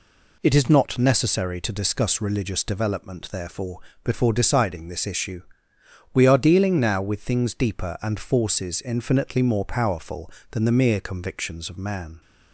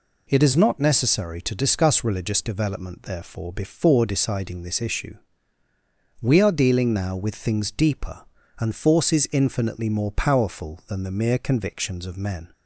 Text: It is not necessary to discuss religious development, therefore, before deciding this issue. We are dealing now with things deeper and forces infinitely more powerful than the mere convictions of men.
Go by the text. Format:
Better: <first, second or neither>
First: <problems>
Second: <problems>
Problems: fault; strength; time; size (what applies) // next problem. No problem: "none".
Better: second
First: says "man" for "men"; at 11.7 s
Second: none